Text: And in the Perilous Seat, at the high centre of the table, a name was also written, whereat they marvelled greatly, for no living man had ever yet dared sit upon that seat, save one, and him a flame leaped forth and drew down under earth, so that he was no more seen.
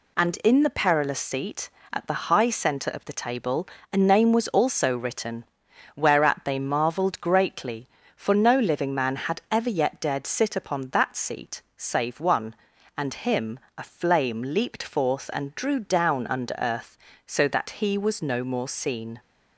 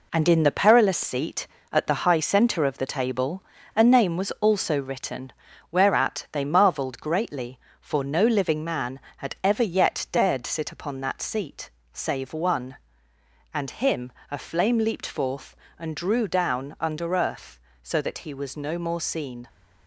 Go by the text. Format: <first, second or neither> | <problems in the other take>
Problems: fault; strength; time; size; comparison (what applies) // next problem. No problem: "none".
first | gets quieter; throughout; 6.5 dB // pauses between "him" and "a"; slight; at 14.1 s; 0.18 s long; slight in the first